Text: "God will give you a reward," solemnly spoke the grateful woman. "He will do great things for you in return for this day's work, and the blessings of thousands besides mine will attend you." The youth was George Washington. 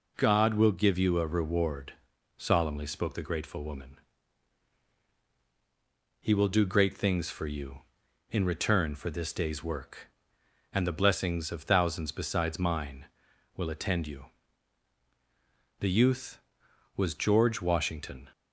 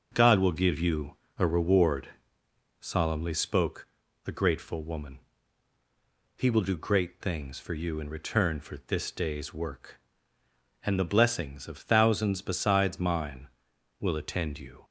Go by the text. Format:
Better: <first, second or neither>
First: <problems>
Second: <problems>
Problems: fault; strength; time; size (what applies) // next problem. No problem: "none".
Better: first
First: none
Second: starts louder than the rest; noticeable; until 1.1 s; 6 dB // pauses between "you" and "a"; slight; at 1.1 s; 0.22 s long // pauses between "spoke" and "the"; at 3.8 s; 0.38 s long // stops before "The youth was George Washington"; at 14.8 s